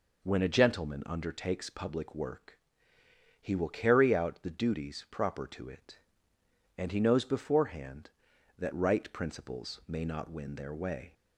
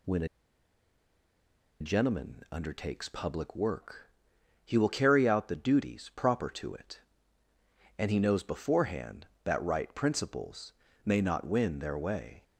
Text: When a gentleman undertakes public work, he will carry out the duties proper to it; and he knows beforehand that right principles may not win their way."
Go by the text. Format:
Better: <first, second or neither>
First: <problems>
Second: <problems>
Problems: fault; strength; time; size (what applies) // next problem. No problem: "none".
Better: first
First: none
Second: pauses between "a" and "gentleman"; strong; at 0.2 s; 1.5 s long // pauses between "principles" and "may"; slight; at 10.7 s; 0.30 s long